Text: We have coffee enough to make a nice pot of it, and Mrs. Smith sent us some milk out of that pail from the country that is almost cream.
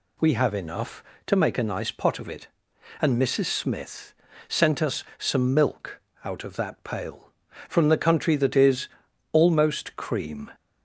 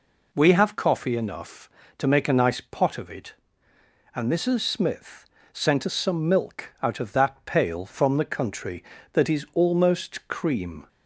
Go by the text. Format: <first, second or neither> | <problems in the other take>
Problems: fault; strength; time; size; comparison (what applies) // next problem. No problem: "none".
second | skips "coffee"; at 0.5 s // pauses between "Smith" and "sent"; slight; at 4.1 s; 0.36 s long; slight in the second // pauses between "milk" and "out"; slight; at 6.0 s; 0.24 s long // pauses between "is" and "almost"; at 8.8 s; 0.44 s long